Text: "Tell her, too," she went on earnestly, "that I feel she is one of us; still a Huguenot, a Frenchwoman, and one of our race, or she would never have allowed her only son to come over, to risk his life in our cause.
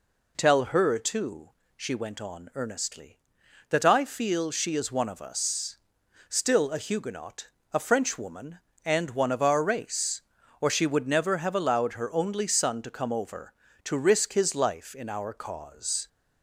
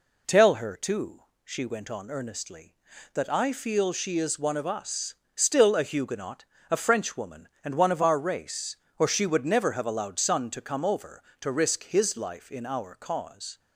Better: first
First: none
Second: skips "her only"; at 10.1 s

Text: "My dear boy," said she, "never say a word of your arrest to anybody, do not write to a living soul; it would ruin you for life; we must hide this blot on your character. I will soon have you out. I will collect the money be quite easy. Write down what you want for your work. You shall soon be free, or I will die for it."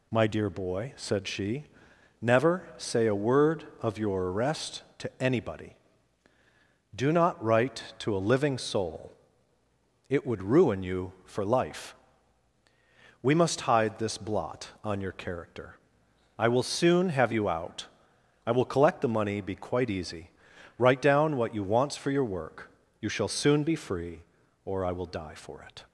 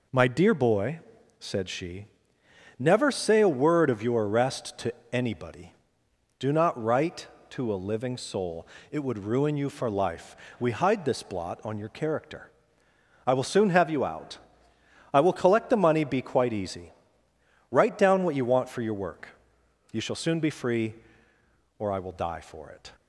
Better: first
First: none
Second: pauses between "to" and "anybody"; slight; at 4.9 s; 0.20 s long // skips "must"; at 10.7 s

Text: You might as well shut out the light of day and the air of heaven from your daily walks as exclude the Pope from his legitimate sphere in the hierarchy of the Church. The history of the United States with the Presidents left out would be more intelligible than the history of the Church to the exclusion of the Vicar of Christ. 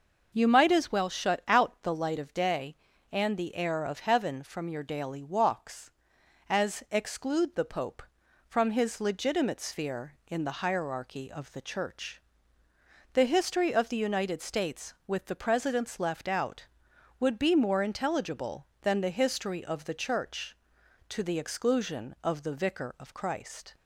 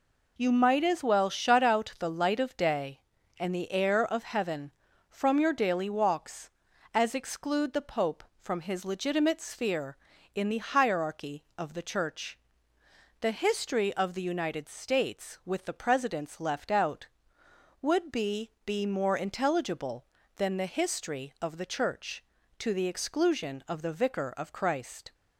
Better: first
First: none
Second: says "be" twice; at 18.6 s

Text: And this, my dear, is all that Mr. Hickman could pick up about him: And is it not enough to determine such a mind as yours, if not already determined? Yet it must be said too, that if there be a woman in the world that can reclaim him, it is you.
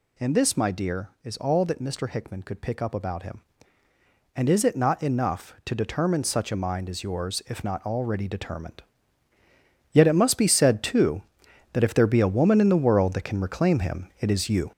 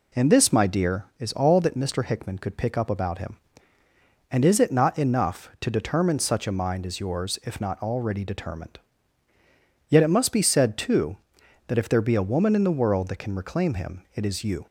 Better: second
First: gets louder; throughout; 6.5 dB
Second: none

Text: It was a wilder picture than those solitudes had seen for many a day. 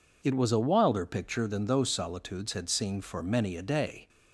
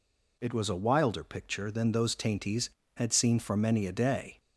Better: first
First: none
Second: says "tainties" for "solitudes"; at 2.1 s

